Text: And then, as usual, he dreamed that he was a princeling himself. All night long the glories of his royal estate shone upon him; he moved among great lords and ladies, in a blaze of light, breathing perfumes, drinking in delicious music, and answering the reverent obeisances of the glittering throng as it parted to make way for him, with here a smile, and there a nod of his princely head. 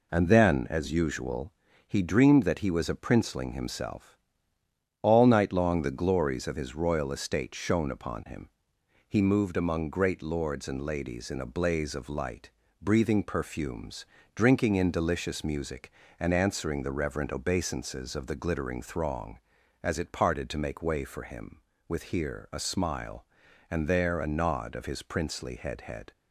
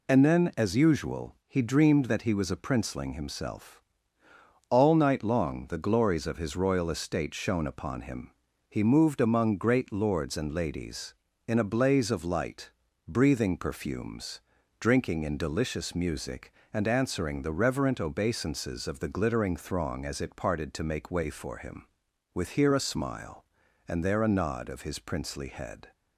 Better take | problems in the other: second | says "head" twice; at 25.8 s

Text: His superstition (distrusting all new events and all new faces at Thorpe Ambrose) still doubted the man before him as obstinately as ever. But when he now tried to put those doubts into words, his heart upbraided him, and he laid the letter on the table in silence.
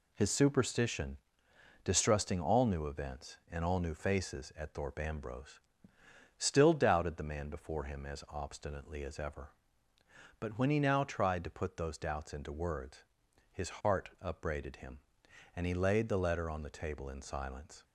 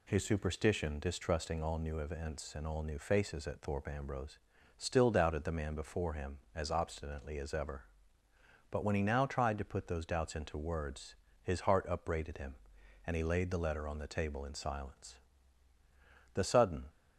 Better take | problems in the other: first | goes on to say "The sudden"; from 16.3 s on; 0.50 s long

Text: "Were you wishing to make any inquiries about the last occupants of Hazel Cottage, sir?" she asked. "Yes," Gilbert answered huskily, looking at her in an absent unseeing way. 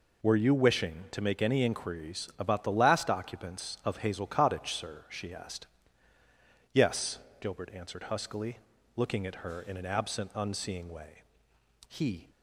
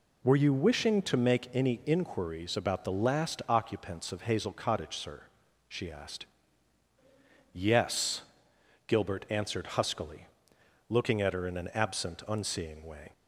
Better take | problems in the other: second | goes on to say "He"; slight; from 11.8 s on; 0.42 s long

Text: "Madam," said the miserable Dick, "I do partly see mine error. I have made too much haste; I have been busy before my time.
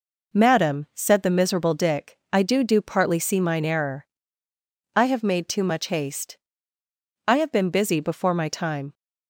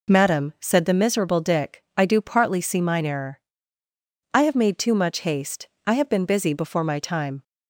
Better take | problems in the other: second | says "do" twice; at 2.6 s

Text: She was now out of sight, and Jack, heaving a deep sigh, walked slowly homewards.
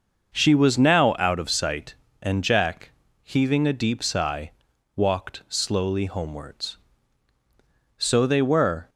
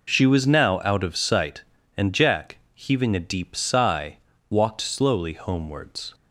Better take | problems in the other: second | goes on to say "So they were"; noticeable; from 7.9 s on; 0.90 s long

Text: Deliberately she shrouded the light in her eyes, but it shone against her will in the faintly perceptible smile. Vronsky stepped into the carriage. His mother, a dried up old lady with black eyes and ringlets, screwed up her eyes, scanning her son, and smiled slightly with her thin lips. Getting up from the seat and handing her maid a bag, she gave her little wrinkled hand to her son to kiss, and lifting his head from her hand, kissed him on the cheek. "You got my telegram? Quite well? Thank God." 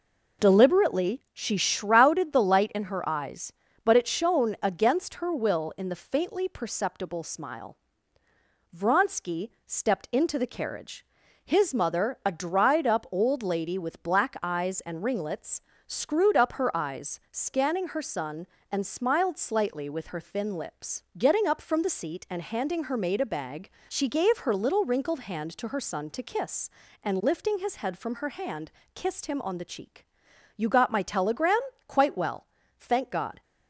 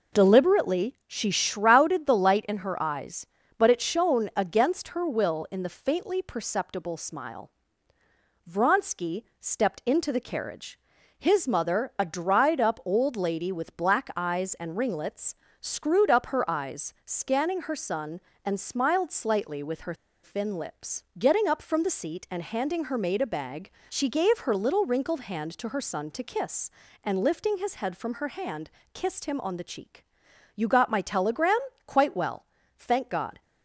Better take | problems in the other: first | pauses between "Vronsky" and "stepped"; slight; at 9.2 s; 0.16 s long; slight in the first // pauses between "her" and "thin"; slight; at 19.9 s; 0.29 s long

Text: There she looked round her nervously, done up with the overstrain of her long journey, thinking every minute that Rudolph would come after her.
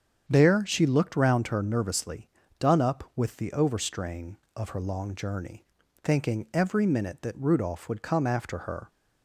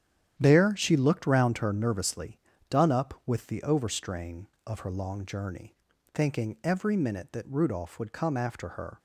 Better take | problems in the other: first | gets quieter; strong; throughout; 10 dB // starts louder than the rest; strong; until 1.3 s; 10 dB; strong in the first

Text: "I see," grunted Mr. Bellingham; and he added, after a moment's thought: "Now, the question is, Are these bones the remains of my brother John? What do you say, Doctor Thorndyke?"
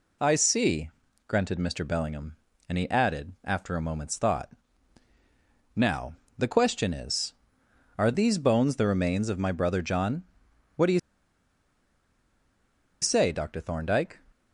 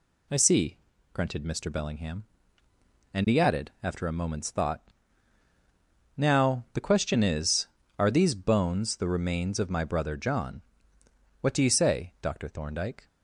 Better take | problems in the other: second | pauses between "you" and "say"; strong; at 10.9 s; 2.0 s long

